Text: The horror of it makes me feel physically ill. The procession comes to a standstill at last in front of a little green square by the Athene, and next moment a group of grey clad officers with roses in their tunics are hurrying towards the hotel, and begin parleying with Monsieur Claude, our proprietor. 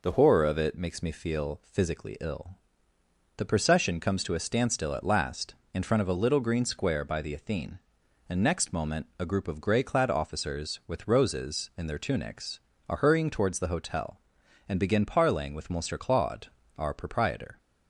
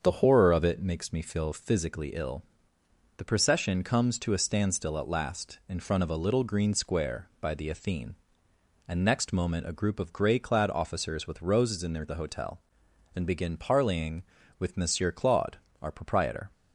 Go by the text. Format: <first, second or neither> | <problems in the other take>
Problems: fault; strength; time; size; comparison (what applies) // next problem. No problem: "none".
first | starts louder than the rest; until 1.0 s; 7 dB // skips "tunics are hurrying towards"; at 12.0 s